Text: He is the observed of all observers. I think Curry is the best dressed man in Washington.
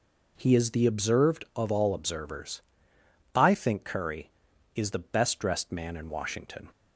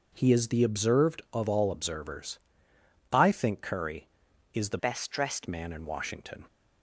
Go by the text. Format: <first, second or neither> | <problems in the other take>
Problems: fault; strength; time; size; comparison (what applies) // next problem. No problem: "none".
first | changes voice from "best" to "dressed"; from 4.7 to 5.4 s; 0.7 s long